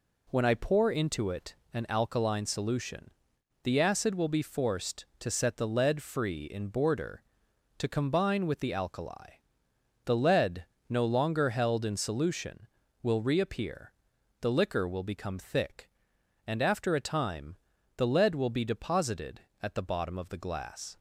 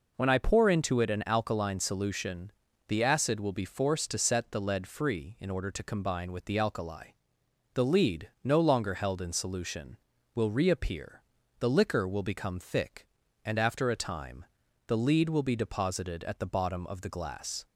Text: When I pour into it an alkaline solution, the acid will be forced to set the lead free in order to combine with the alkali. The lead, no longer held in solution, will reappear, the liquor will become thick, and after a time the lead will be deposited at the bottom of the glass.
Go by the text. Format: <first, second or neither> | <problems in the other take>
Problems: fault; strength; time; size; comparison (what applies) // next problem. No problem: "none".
second | pauses between "it" and "an"; slight; at 1.5 s; 0.18 s long // says "border" for "order"; at 6.6 s // pauses between "time" and "the"; at 17.5 s; 0.40 s long; also in the second